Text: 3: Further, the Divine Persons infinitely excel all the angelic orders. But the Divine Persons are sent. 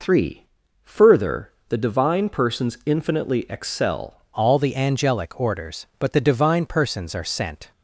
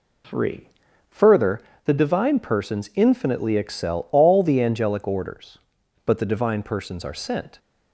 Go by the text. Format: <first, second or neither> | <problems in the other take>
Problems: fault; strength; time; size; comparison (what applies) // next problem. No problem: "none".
second | changes voice at "all"; from 4.3 s on; 3.4 s long